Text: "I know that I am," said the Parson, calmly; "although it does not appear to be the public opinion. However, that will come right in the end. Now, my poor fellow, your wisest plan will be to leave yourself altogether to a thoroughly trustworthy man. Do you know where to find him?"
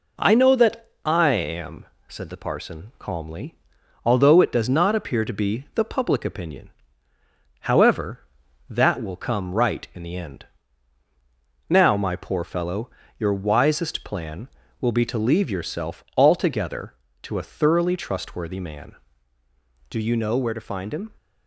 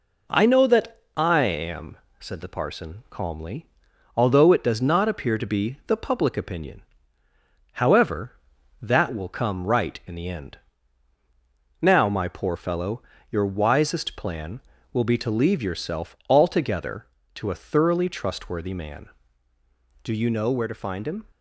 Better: neither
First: pauses between "that" and "I"; slight; at 0.9 s; 0.16 s long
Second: pauses between "that" and "I"; slight; at 1.0 s; 0.16 s long

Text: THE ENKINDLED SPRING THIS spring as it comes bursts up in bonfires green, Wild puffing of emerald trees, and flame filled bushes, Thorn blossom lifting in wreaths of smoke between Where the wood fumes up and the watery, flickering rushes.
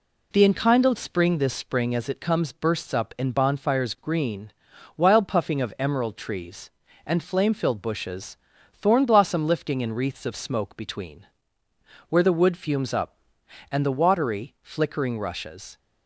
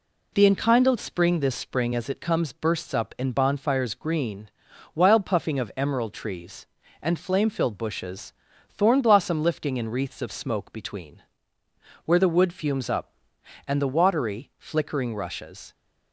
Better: neither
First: pauses between "between" and "Where"; noticeable; at 11.2 s; 0.82 s long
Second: pauses between "between" and "Where"; noticeable; at 11.2 s; 0.82 s long

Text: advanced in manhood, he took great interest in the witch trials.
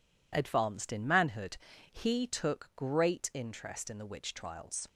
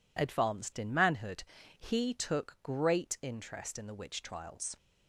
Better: neither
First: none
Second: none

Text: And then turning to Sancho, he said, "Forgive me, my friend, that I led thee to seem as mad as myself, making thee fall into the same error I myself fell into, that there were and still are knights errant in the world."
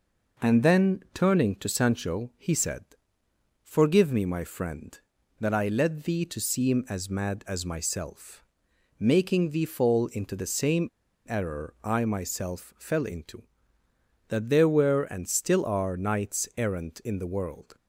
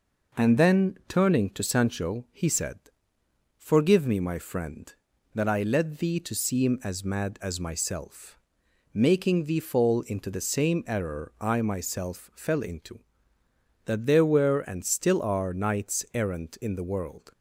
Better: second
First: pauses between "same" and "error"; at 10.8 s; 0.40 s long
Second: none

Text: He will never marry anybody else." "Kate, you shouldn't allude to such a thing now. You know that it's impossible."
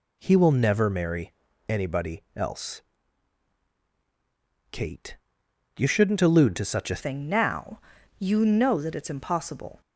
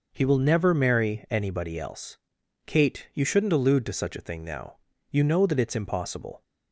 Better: second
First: pauses between "marry" and "anybody"; slight; at 1.3 s; 0.36 s long // changes voice at "thing"; from 6.9 s on; 2.9 s long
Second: none

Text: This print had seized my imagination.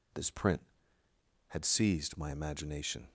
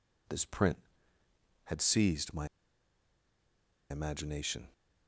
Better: first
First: none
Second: pauses between "my" and "imagination"; strong; at 2.4 s; 1.4 s long

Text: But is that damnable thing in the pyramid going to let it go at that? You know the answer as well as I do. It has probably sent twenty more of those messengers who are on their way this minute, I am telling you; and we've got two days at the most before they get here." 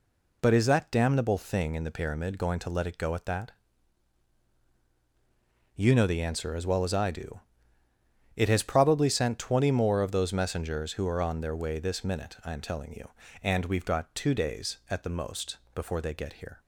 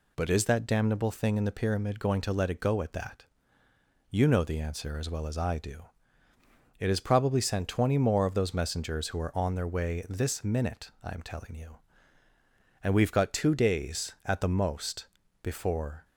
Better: first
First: pauses between "most" and "before"; slight; at 15.5 s; 0.18 s long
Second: pauses between "most" and "before"; slight; at 15.0 s; 0.36 s long // stops before "they get here"; at 16.0 s

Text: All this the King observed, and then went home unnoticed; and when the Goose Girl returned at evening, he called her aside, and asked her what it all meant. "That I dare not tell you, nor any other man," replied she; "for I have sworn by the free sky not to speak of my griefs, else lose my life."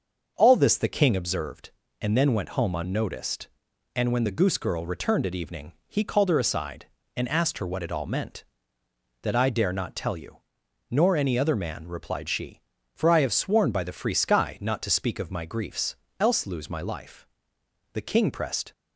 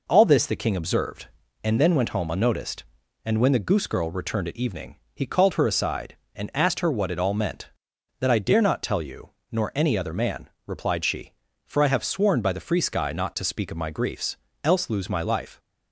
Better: second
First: starts louder than the rest; until 1.3 s; 6.5 dB // goes on to say "The King pressed"; noticeable; from 17.9 s on; 0.78 s long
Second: none

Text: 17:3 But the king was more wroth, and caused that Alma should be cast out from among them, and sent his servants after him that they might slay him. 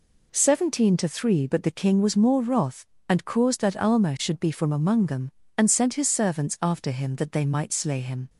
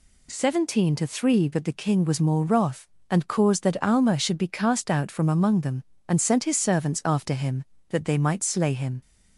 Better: second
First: skips "cast out"; at 4.4 s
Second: none

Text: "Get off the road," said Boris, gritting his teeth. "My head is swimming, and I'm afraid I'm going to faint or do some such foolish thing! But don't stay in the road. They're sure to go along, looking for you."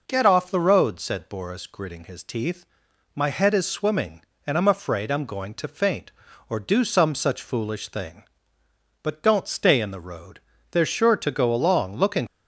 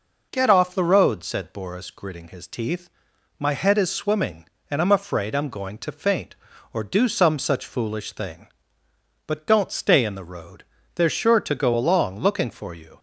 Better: second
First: stops before "for you"; at 12.2 s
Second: none

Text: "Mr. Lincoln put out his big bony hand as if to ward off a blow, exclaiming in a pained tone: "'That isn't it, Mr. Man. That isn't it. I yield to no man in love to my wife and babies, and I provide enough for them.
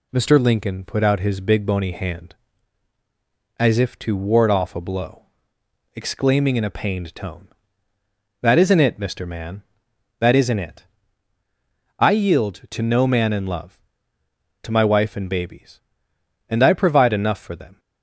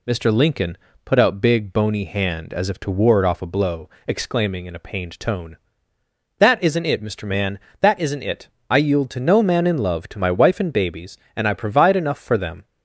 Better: first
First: none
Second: pauses between "Lincoln" and "put"; slight; at 0.7 s; 0.26 s long // skips "his"; at 1.4 s

